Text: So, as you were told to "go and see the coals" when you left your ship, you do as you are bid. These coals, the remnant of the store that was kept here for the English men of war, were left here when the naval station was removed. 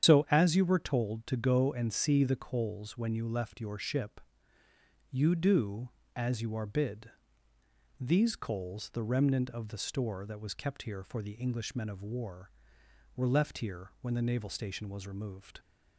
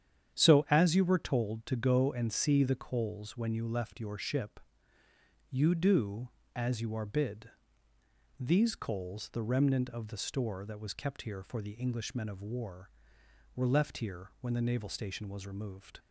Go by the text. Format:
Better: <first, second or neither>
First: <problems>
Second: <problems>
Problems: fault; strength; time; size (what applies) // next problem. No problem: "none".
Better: second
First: loses the start of "So"; at 0.0 s; 80 ms // starts louder than the rest; strong; until 1.1 s; 9 dB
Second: starts louder than the rest; strong; until 1.4 s; 9.5 dB